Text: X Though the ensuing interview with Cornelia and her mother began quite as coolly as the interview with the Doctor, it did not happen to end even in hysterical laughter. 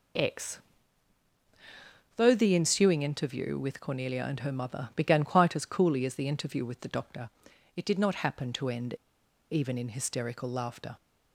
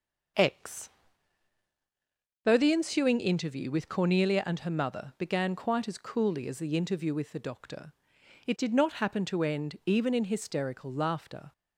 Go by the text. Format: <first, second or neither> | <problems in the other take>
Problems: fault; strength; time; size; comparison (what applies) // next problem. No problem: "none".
second | pauses between "X" and "Though"; strong; at 0.6 s; 1.5 s long; strong in the second // pauses between "end" and "even"; noticeable; at 8.9 s; 0.56 s long